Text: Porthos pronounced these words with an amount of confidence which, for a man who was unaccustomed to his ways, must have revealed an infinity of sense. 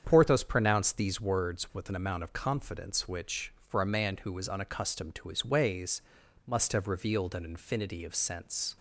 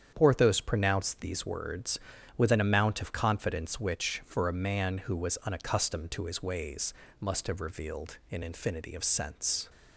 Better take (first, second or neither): neither